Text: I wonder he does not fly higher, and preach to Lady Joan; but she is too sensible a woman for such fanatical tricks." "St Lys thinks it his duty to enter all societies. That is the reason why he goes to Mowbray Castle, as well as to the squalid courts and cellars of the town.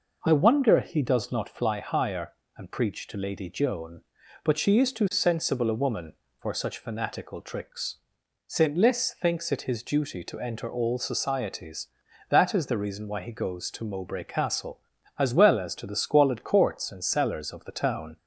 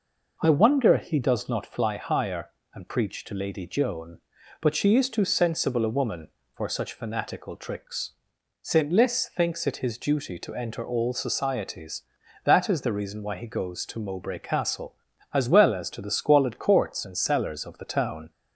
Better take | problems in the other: neither | none

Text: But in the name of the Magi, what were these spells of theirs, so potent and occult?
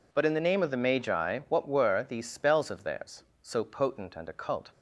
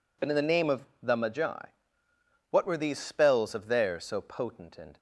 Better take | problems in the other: first | pauses between "of" and "the"; slight; at 0.8 s; 0.18 s long // stops before "occult"; at 4.9 s

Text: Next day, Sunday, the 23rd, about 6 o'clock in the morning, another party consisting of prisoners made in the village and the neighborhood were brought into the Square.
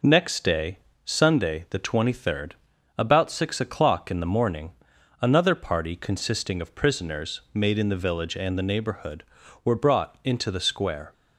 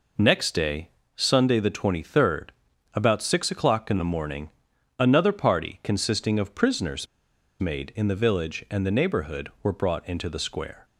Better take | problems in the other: first | pauses between "prisoners" and "made"; noticeable; at 7.0 s; 0.54 s long

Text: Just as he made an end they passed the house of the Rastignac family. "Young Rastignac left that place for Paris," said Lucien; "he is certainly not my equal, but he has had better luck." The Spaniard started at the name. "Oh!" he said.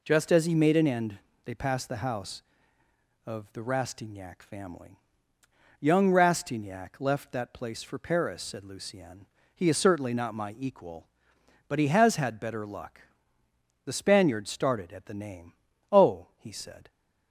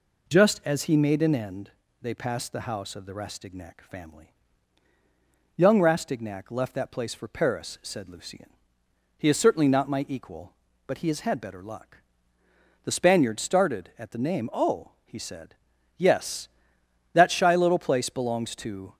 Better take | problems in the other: first | pauses between "end" and "they"; slight; at 1.7 s; 0.32 s long; slight in the first // goes on to say "Yes That shy little place belongs to"; strong; from 15.9 s on; 3.0 s long

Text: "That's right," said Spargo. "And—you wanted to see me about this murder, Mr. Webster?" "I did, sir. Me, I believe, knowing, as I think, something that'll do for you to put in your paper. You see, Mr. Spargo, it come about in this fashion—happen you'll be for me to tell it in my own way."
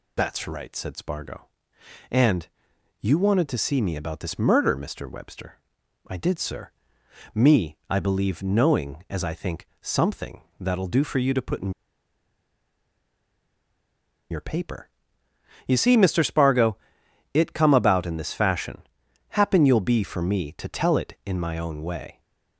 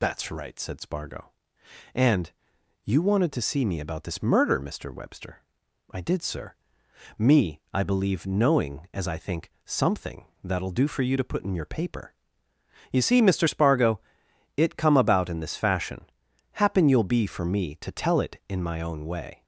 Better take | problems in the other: second | pauses between "something" and "that'll"; slight; at 10.4 s; 0.16 s long; slight in the second // pauses between "in" and "your"; strong; at 11.7 s; 2.5 s long

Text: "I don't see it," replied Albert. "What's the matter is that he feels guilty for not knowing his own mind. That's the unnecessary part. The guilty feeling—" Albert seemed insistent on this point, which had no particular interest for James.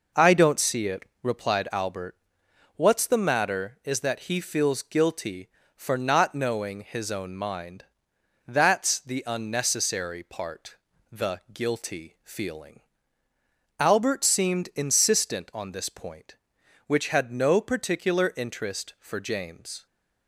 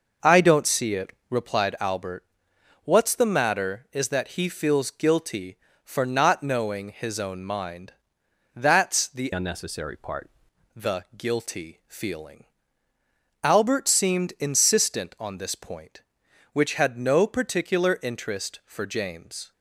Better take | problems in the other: first | changes voice from "unnecessary" to "part"; from 9.3 to 10.3 s; 1.0 s long

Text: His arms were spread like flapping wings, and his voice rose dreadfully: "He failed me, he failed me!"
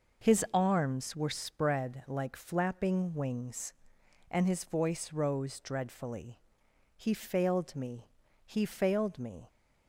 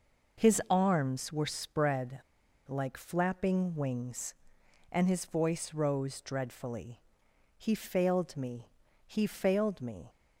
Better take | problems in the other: first | pauses between "spread" and "like"; noticeable; at 2.2 s; 0.47 s long

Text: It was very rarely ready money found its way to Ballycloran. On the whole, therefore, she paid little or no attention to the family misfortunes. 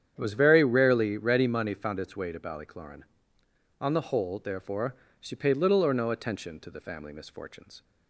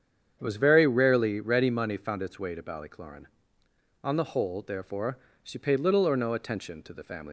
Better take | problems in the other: first | starts louder than the rest; strong; until 1.4 s; 8 dB; strong in the first // stops before "misfortunes"; at 7.2 s

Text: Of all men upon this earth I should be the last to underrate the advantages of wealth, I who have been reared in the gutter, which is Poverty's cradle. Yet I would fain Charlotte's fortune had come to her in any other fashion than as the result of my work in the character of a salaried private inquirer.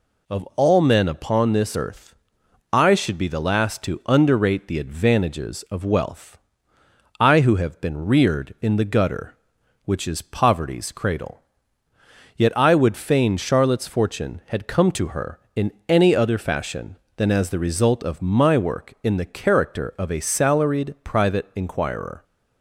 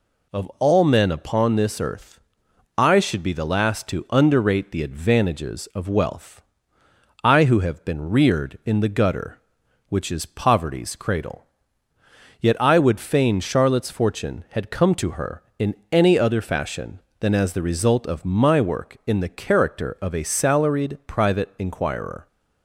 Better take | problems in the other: neither | pauses between "earth" and "I"; noticeable; the same in both // pauses between "in" and "any"; slight; the same in both

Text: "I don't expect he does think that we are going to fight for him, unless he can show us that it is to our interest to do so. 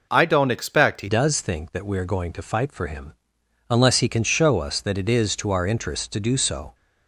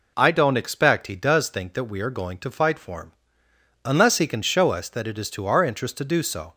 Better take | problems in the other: second | changes voice at "does"; from 1.0 s on; 5.7 s long

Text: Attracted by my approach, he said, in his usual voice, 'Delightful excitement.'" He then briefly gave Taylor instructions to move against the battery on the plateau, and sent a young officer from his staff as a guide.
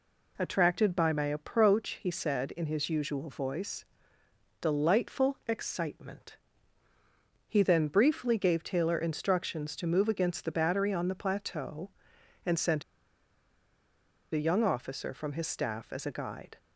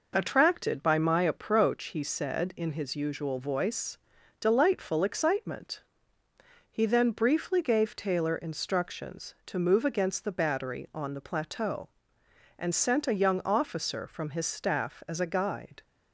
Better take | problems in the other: second | pauses between "sent" and "a"; strong; at 12.8 s; 1.5 s long

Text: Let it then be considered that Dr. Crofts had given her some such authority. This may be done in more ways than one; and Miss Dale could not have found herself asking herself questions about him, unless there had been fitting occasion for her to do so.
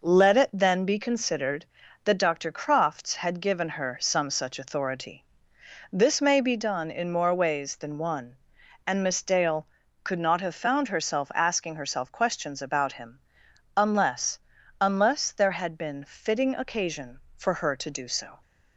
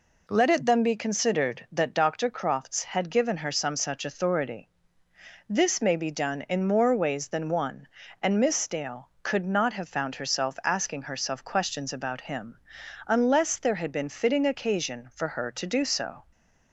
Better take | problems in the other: second | says "unless" twice; at 14.8 s

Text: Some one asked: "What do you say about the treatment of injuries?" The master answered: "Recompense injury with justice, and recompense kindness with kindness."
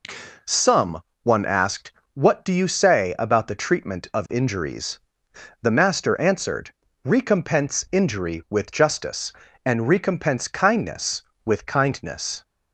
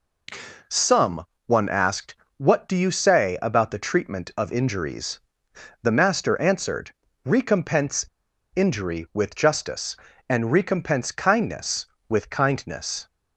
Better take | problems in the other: first | pauses between "Some" and "one"; slight; at 1.2 s; 0.22 s long; slight in the first // pauses between "Recompense" and "injury"; noticeable; at 8.0 s; 0.51 s long

